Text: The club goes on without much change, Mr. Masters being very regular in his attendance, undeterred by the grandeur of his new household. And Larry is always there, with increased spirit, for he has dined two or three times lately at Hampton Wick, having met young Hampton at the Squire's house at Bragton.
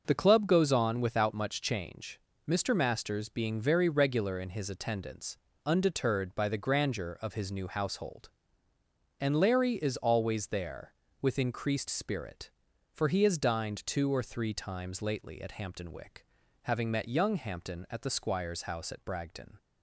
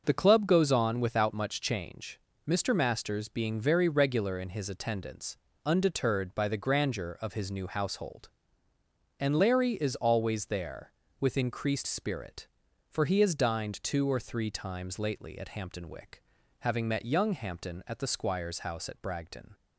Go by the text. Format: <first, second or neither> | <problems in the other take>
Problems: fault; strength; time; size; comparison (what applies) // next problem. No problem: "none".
neither | none